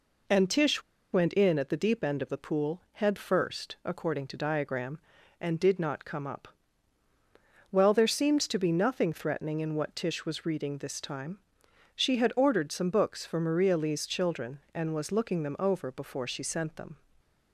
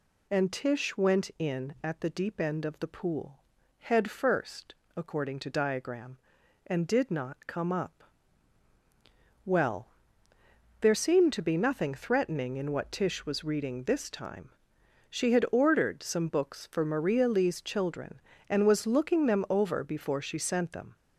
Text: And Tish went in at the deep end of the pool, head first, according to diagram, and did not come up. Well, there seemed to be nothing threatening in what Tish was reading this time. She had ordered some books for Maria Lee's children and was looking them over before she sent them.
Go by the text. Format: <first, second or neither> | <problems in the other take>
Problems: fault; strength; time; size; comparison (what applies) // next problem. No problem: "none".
second | pauses between "Tish" and "went"; slight; at 0.8 s; 0.31 s long